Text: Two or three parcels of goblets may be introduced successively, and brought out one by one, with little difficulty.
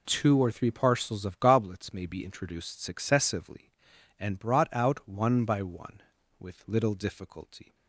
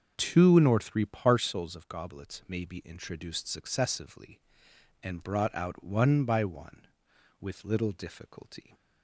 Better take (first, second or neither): first